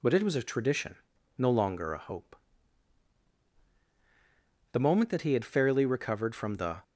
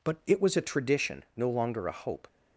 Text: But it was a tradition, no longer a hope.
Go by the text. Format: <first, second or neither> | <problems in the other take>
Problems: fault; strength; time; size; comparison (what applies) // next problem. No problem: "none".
second | goes on to say "The moment that he had fairly recovered from the"; strong; from 4.7 s on; 2.1 s long